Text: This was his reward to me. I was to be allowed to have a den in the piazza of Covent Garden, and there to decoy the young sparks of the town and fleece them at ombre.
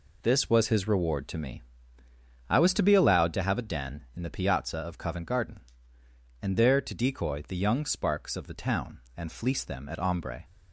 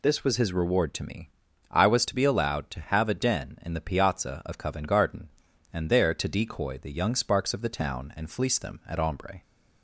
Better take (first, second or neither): neither